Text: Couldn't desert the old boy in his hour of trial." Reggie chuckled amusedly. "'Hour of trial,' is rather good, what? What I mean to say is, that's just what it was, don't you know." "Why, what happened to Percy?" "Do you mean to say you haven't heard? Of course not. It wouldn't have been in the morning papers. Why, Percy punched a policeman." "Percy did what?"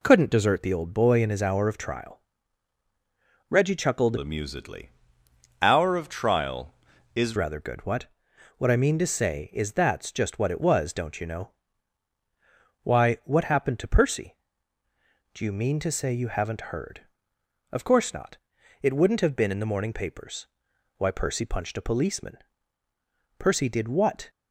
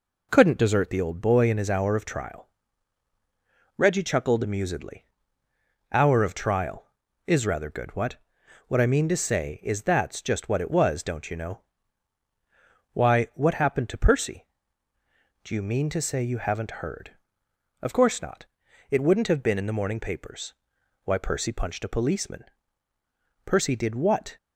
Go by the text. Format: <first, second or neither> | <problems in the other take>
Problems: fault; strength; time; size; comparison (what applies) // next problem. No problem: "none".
second | changes voice from "amusedly" to "is"; from 4.1 to 7.3 s; 3.2 s long